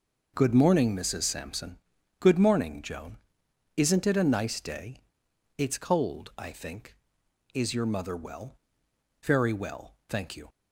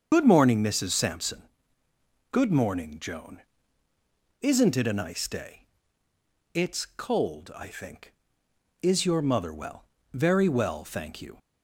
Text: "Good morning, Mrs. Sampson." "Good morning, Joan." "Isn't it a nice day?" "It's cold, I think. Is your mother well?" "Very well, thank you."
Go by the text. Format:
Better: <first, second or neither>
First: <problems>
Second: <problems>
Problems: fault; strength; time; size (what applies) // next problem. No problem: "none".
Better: first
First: none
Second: loses the start of "Good"; at 0.1 s; 60 ms // starts louder than the rest; until 1.1 s; 7 dB